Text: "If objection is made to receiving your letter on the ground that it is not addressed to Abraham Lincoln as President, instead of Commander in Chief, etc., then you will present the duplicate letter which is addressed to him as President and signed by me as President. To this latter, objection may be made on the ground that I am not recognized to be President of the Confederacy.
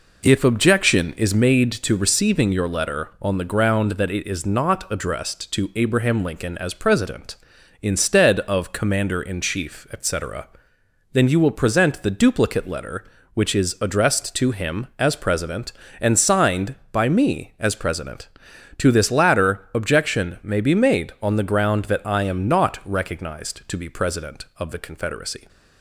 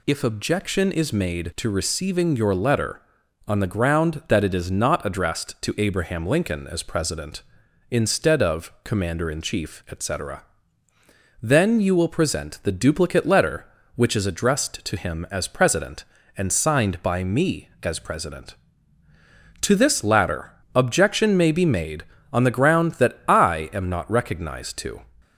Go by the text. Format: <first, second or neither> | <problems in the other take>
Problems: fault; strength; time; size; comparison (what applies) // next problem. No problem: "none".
first | stops before "be President of the Confederacy"; at 25.2 s